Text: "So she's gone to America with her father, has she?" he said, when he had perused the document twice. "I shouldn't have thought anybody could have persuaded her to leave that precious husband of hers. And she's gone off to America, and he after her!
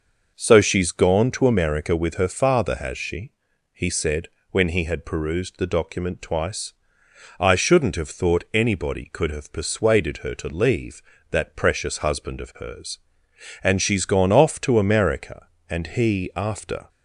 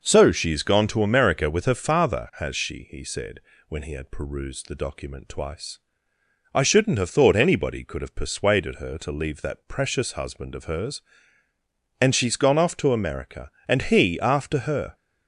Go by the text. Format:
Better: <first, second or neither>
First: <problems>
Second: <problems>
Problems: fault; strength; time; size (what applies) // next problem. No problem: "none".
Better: second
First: stops before "her"; at 16.8 s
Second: none